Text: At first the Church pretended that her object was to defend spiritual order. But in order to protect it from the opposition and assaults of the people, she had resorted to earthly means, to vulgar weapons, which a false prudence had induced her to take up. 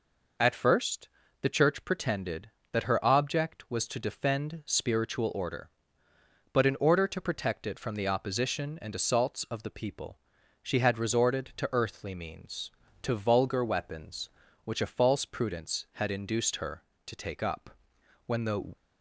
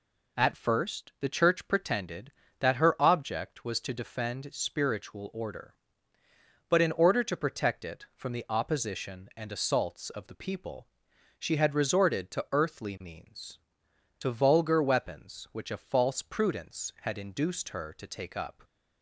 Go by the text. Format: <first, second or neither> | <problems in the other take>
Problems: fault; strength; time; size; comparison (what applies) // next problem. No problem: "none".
second | pauses between "first" and "the"; slight; at 1.0 s; 0.34 s long // goes on to say "When the"; from 18.2 s on; 0.50 s long